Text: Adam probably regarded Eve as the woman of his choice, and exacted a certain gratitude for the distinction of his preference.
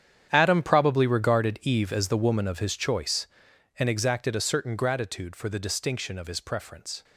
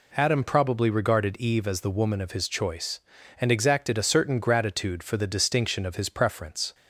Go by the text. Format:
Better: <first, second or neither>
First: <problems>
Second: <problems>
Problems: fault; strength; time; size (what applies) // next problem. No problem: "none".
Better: second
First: gets quieter; strong; throughout; 14.5 dB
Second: none